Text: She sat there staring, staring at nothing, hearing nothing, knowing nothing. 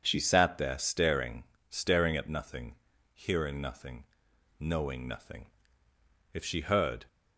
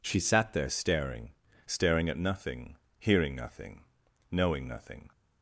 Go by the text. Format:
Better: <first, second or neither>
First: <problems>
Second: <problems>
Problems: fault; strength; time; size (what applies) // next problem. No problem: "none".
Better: second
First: goes on to say "If she heard"; noticeable; from 6.3 s on; 0.72 s long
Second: none